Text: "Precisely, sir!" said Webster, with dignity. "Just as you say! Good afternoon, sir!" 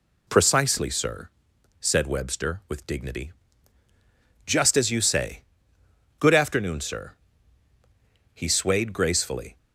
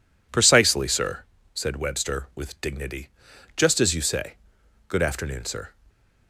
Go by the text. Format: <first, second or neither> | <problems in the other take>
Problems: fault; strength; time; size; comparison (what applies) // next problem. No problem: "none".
second | goes on to say "He swayed gracefully"; noticeable; from 8.3 s on; 1.2 s long